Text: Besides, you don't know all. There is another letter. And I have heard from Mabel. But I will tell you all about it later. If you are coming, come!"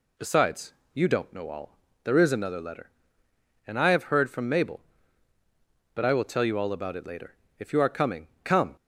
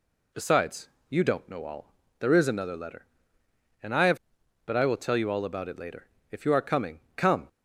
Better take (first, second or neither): first